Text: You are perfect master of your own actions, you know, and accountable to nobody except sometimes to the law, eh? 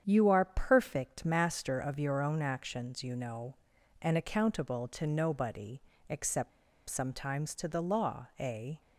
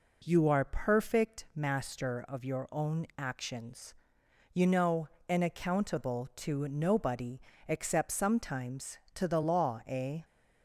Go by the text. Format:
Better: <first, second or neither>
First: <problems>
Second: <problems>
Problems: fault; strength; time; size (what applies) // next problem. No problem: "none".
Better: second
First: starts louder than the rest; strong; until 1.0 s; 8 dB // pauses between "nobody" and "except"; slight; at 5.8 s; 0.30 s long // pauses between "except" and "sometimes"; at 6.5 s; 0.37 s long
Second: pauses between "nobody" and "except"; slight; at 7.3 s; 0.28 s long